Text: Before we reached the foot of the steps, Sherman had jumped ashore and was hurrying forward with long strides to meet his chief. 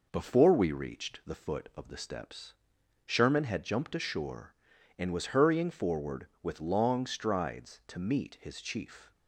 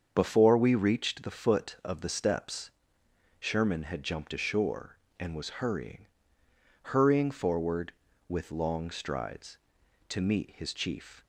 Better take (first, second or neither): first